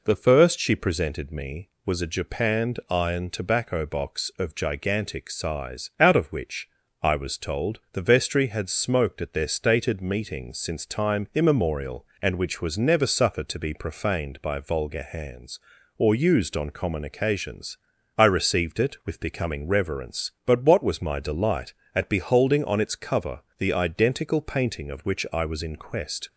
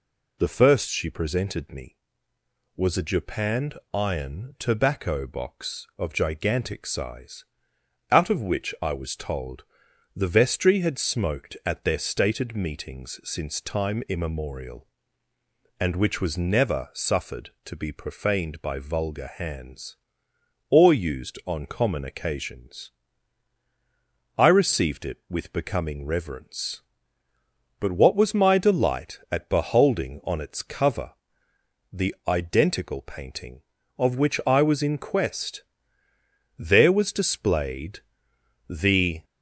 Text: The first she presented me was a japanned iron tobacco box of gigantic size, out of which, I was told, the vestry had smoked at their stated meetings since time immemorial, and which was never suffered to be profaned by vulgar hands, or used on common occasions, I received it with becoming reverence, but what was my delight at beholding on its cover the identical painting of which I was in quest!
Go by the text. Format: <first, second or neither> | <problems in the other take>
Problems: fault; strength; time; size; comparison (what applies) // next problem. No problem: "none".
first | pauses between "japanned" and "iron"; slight; at 3.7 s; 0.16 s long // pauses between "cover" and "the"; noticeable; at 31.1 s; 0.80 s long; slight in the first // goes on to say "There was displayed the"; strong; from 36.5 s on; 2.6 s long